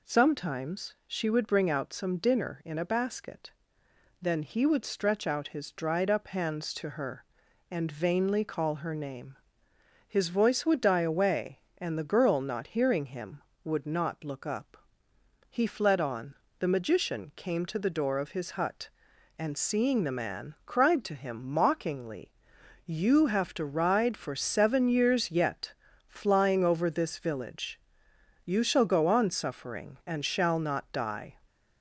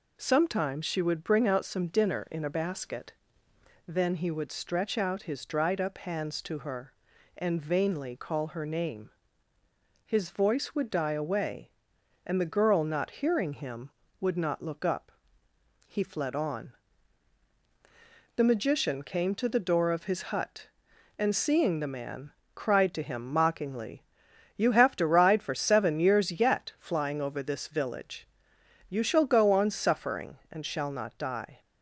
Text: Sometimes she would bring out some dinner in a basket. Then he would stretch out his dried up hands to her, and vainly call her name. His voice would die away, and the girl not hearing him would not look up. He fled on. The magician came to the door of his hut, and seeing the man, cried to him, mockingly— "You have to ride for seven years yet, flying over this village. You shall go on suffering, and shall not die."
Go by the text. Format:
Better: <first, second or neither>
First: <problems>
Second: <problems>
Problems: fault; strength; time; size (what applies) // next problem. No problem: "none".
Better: neither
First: none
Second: none